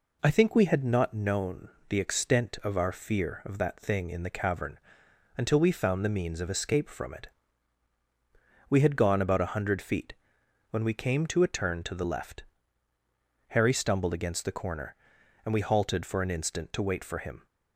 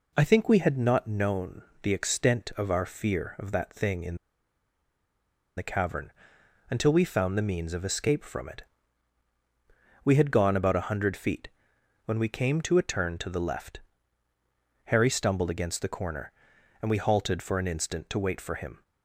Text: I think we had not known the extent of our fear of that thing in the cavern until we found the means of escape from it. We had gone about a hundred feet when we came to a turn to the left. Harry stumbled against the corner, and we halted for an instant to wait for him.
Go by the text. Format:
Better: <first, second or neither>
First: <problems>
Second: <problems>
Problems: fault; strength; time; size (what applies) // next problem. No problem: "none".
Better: first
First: pauses between "known" and "the"; slight; at 1.6 s; 0.18 s long // pauses between "cavern" and "until"; noticeable; at 4.7 s; 0.60 s long // pauses between "feet" and "when"; noticeable; at 10.1 s; 0.58 s long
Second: pauses between "known" and "the"; slight; at 1.6 s; 0.18 s long // pauses between "in" and "the"; strong; at 4.1 s; 1.4 s long // pauses between "cavern" and "until"; noticeable; at 6.1 s; 0.60 s long // pauses between "feet" and "when"; noticeable; at 11.4 s; 0.58 s long